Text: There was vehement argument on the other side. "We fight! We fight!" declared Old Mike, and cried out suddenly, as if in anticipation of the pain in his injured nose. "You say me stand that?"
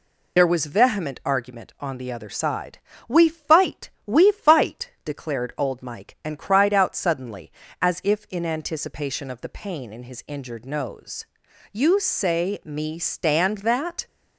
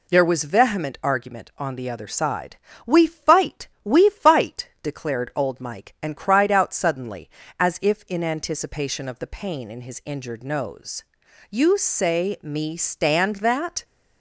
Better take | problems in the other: second | loses the start of "There"; at 0.3 s; 60 ms

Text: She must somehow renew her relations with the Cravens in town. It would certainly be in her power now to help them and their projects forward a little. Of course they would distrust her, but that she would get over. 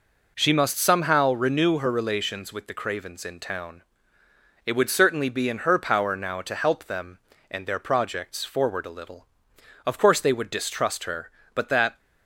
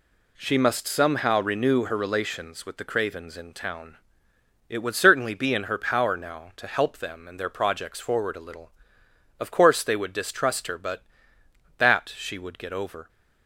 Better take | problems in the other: second | stops before "she would get over"; at 11.9 s

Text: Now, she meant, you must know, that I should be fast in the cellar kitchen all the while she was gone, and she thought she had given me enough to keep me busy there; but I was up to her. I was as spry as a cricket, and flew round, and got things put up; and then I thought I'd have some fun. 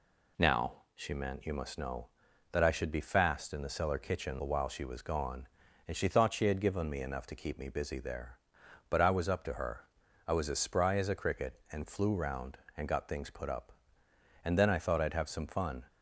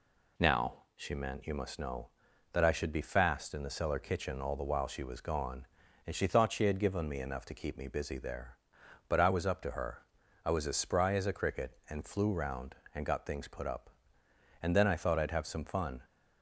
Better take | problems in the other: second | skips "all"; at 4.3 s

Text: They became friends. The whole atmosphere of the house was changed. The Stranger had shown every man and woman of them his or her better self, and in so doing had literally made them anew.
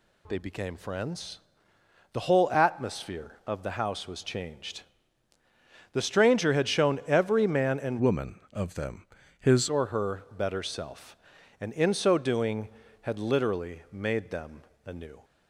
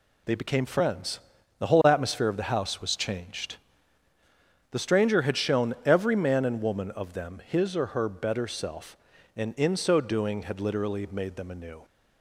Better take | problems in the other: second | changes voice from "woman" to "his"; from 7.9 to 9.6 s; 1.7 s long // pauses between "them" and "his"; slight; at 9.0 s; 0.32 s long // pauses between "them" and "anew"; slight; at 14.6 s; 0.22 s long

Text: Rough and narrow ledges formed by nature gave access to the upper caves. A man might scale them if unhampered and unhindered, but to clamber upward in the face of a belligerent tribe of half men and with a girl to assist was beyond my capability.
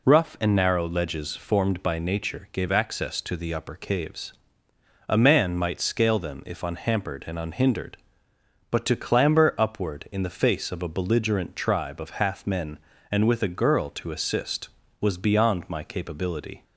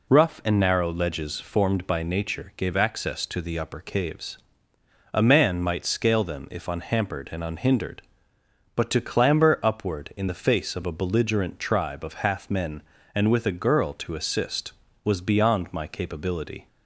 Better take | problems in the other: neither | none

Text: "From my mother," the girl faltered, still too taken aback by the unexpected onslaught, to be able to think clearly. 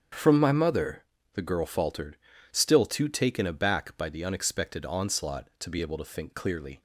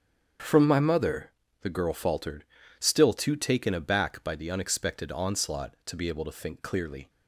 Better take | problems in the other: neither | starts louder than the rest; strong; the same in both

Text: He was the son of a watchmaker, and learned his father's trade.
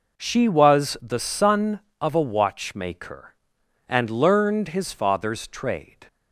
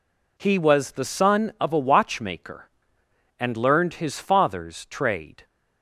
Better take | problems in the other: second | says "She" for "He"; at 0.1 s

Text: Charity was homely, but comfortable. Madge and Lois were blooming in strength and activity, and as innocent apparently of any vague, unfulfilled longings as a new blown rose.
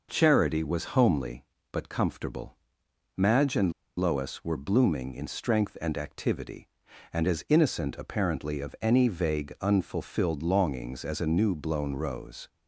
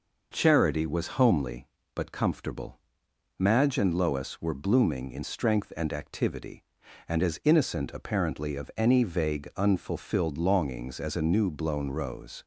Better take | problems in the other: second | pauses between "and" and "Lois"; slight; at 3.7 s; 0.25 s long

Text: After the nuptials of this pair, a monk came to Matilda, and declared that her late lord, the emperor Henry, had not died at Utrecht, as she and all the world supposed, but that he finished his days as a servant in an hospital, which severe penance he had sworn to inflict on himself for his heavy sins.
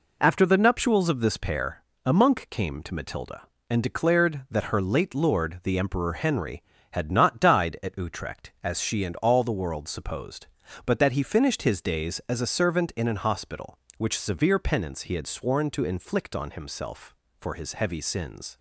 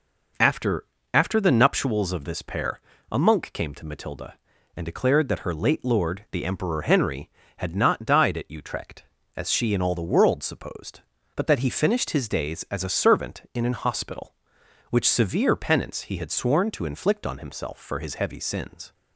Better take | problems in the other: first | says "After" twice; at 1.1 s

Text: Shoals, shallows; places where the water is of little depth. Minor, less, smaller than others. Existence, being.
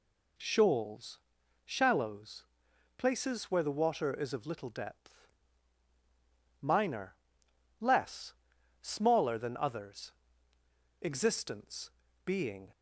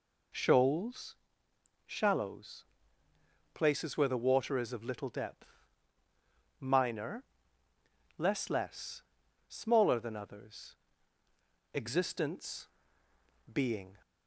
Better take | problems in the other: first | says "less" twice; at 8.4 s

